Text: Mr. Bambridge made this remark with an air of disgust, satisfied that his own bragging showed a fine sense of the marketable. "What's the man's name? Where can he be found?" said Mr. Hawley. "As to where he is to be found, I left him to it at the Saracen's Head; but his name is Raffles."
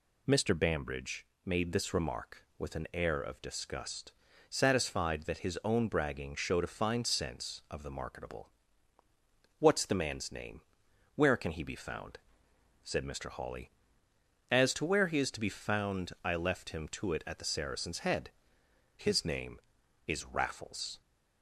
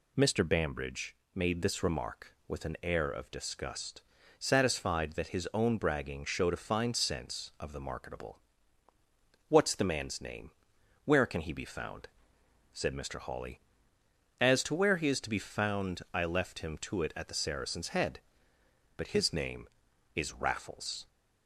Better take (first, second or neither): second